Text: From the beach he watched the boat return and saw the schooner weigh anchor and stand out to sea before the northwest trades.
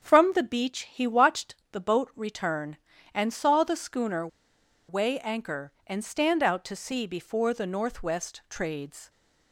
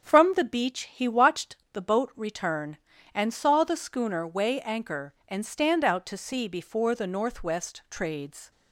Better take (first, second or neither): second